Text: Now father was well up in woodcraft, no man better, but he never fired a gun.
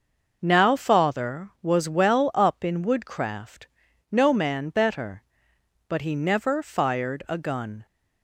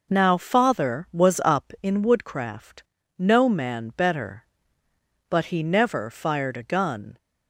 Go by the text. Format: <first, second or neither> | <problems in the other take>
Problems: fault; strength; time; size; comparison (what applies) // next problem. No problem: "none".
first | skips "well"; at 1.4 s